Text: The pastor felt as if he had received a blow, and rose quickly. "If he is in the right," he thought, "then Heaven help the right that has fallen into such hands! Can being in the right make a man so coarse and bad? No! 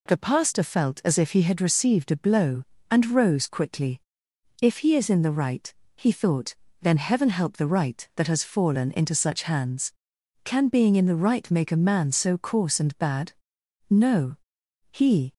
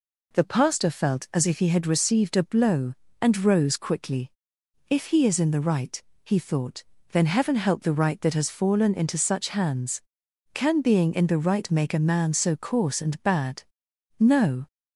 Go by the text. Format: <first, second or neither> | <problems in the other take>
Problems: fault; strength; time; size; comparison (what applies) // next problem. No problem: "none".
second | goes on to say "He"; slight; from 14.9 s on; 0.40 s long